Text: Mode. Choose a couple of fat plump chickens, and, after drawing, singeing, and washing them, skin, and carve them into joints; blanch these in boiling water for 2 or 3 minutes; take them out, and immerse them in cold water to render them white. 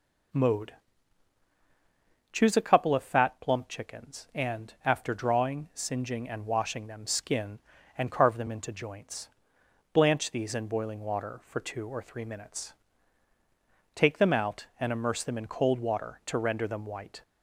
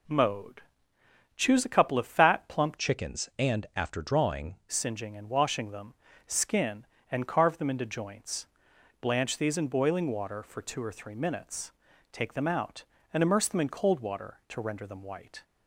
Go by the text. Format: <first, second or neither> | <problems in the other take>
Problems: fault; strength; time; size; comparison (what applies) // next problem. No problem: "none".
first | changes voice from "chickens" to "drawing"; from 2.7 to 4.5 s; 1.8 s long